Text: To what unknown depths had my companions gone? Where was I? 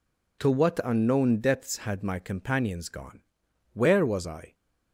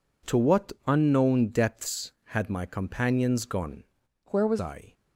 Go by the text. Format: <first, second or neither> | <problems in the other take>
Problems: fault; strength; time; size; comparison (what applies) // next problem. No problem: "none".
first | changes voice from "Where" to "was"; from 4.2 to 4.5 s; 0.3 s long